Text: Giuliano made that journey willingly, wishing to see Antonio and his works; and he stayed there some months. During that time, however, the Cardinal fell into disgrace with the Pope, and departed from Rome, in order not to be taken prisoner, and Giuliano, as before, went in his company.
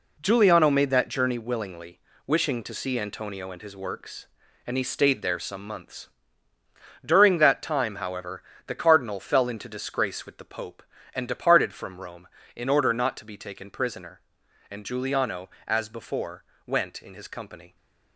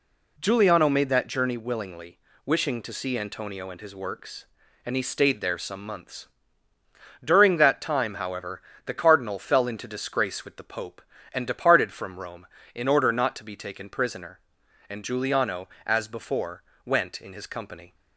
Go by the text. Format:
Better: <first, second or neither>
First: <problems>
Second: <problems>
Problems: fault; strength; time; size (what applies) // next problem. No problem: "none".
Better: second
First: gets quieter; strong; throughout; 8.5 dB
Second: none